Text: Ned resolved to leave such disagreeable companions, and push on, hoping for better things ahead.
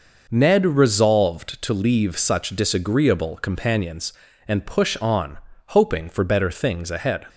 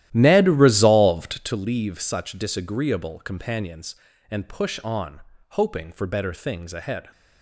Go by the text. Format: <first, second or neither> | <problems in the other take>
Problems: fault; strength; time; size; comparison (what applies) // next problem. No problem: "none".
first | starts louder than the rest; strong; until 1.6 s; 13.5 dB